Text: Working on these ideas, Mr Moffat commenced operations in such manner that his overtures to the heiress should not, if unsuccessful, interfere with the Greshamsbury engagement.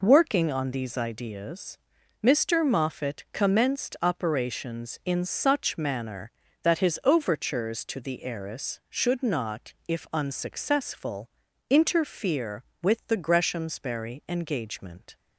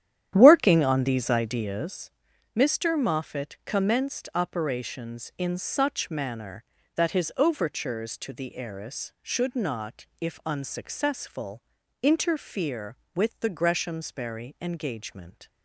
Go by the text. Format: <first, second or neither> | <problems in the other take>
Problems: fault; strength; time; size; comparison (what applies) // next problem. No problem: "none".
first | starts louder than the rest; strong; until 2.0 s; 10.5 dB